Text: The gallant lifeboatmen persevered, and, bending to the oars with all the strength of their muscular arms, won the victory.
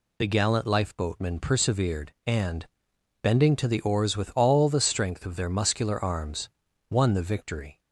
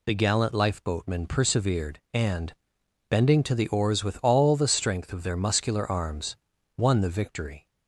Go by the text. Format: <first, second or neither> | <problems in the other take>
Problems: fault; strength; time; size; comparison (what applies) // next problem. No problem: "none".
neither | none